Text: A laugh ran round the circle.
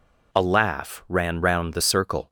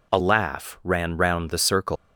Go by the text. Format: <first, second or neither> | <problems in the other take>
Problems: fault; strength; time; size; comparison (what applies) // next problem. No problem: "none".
first | leaves "circle" unfinished; at 1.9 s; 110 ms